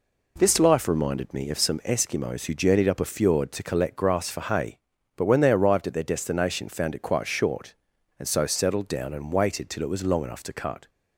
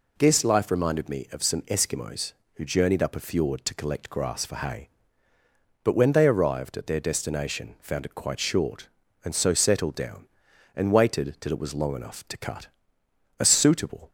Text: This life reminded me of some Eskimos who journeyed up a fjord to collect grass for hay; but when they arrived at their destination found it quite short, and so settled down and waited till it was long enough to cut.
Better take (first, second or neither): first